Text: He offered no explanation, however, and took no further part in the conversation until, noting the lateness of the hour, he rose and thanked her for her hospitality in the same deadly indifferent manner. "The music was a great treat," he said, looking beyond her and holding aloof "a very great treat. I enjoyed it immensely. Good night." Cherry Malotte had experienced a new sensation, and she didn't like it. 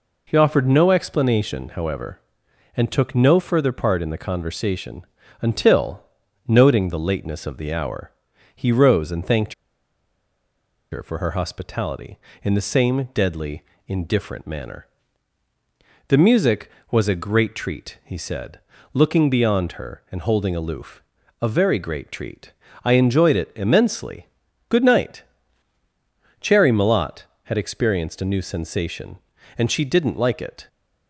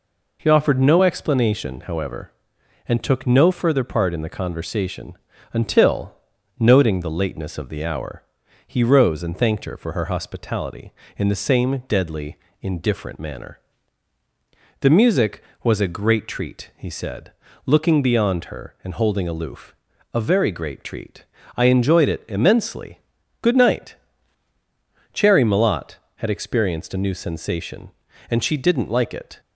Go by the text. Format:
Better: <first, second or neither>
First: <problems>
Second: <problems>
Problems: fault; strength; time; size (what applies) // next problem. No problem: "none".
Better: second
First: pauses between "conversation" and "until"; slight; at 5.0 s; 0.34 s long // pauses between "thanked" and "her"; strong; at 9.5 s; 1.3 s long // pauses between "deadly" and "indifferent"; slight; at 13.6 s; 0.24 s long // pauses between "aloof" and "a"; at 21.0 s; 0.40 s long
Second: pauses between "conversation" and "until"; slight; at 5.1 s; 0.34 s long // pauses between "deadly" and "indifferent"; slight; at 12.3 s; 0.24 s long // pauses between "aloof" and "a"; at 19.7 s; 0.40 s long